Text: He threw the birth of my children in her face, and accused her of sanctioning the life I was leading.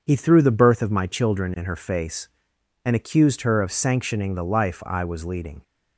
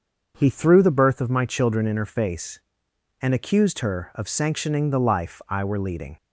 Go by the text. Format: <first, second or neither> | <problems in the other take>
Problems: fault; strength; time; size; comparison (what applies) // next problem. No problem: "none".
first | starts louder than the rest; until 1.3 s; 6.5 dB // says "were" for "was"; at 5.6 s